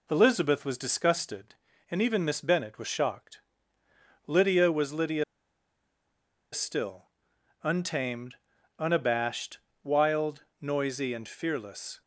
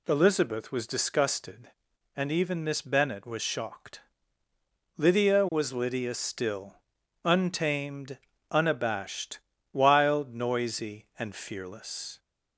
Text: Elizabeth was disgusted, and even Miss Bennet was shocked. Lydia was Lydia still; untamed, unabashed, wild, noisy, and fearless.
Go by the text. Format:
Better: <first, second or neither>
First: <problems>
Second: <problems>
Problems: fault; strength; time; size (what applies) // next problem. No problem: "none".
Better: second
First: pauses between "Lydia" and "still"; strong; at 5.2 s; 1.2 s long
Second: none